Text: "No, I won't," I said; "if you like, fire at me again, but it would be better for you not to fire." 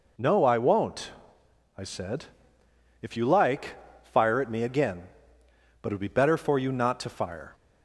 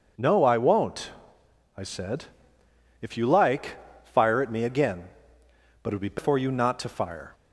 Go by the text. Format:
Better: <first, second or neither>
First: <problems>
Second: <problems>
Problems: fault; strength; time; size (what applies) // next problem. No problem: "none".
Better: first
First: none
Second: skips "better"; at 6.1 s